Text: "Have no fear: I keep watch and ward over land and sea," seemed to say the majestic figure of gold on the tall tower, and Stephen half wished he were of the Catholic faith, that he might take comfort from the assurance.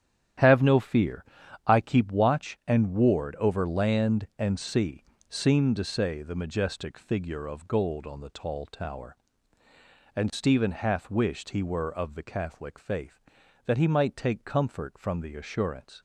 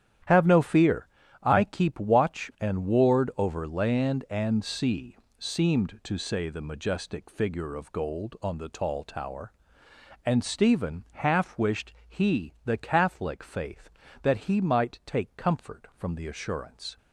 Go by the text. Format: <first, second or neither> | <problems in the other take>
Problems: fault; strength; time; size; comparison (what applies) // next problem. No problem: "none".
first | starts louder than the rest; strong; until 1.6 s; 10.5 dB; strong in the first // pauses between "wished" and "he"; slight; at 11.9 s; 0.16 s long // skips "were of"; at 12.5 s